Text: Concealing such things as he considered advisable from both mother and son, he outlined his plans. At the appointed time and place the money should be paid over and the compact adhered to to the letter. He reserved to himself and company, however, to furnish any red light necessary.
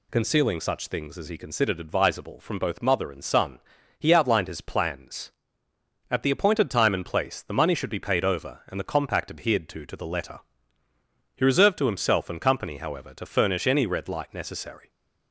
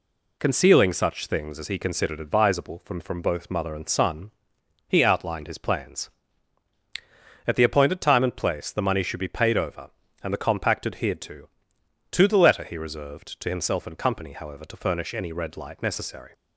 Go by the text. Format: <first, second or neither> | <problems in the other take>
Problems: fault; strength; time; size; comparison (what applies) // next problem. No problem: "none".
first | says "from" twice; at 2.9 s